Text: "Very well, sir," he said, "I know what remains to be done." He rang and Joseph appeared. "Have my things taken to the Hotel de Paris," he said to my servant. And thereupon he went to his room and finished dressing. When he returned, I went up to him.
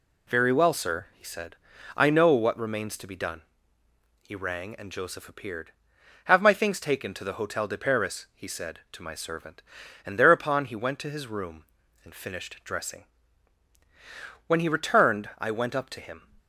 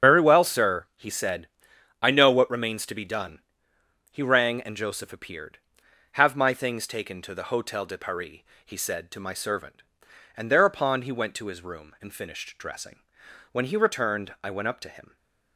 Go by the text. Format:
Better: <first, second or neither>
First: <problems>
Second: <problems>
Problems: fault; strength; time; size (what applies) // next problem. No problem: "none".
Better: first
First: none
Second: loses the start of "Very"; at 0.0 s; 95 ms // starts louder than the rest; strong; until 1.1 s; 7.5 dB